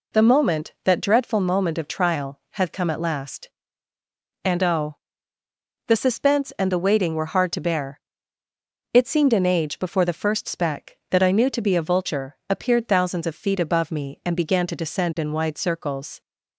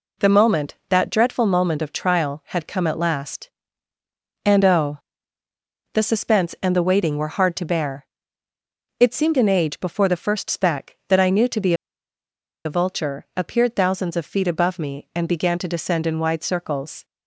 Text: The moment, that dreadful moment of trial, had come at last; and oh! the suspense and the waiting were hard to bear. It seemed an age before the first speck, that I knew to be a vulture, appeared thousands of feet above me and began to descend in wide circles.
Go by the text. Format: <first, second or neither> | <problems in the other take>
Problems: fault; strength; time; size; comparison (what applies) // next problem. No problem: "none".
first | pauses between "be" and "a"; noticeable; at 11.7 s; 0.91 s long